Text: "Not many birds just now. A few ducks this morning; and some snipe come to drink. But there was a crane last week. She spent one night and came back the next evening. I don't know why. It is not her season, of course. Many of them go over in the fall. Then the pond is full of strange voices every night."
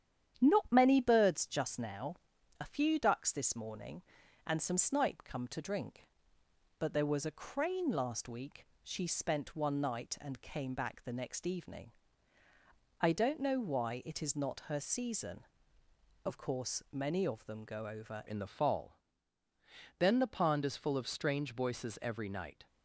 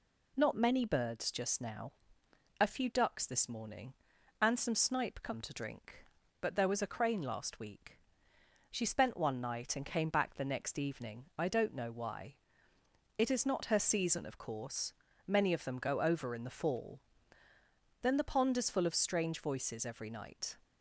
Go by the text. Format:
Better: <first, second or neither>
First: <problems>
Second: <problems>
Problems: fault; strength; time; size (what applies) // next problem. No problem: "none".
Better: second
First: starts louder than the rest; strong; until 1.4 s; 9.5 dB // changes voice at "in"; from 18.2 s on; 4.4 s long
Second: none